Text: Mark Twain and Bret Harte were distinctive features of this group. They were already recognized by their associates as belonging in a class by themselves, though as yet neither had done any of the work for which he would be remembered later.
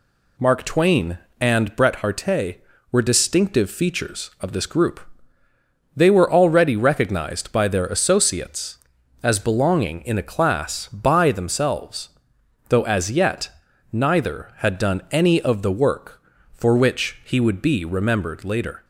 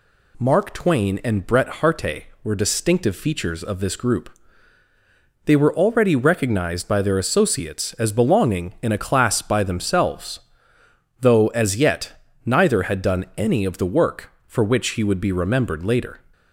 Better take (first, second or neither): neither